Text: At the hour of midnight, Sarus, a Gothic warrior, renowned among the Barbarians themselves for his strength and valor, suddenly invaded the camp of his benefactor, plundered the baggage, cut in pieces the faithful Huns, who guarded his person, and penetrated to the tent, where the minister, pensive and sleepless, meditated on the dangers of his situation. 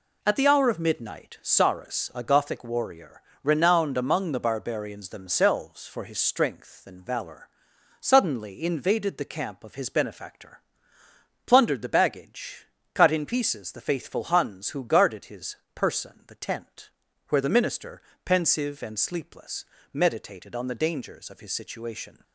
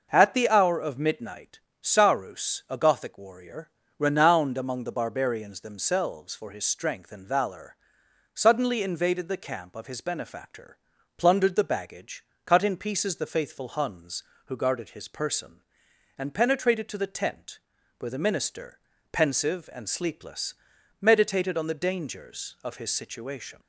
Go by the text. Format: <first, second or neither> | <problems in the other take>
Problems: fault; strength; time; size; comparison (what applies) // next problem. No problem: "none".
second | pauses between "his" and "person"; slight; at 15.5 s; 0.16 s long // skips "and penetrated to"; at 16.2 s